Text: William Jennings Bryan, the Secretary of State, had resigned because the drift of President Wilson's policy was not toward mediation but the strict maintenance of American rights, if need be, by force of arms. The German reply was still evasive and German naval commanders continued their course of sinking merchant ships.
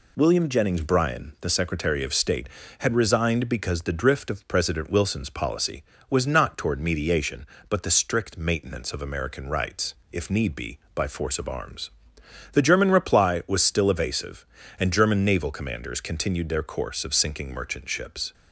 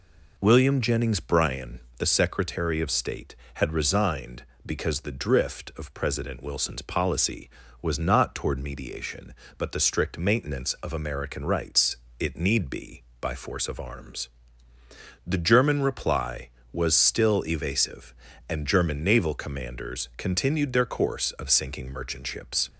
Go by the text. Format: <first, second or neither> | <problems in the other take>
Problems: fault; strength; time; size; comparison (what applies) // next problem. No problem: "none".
first | says "it" for "if"; at 12.1 s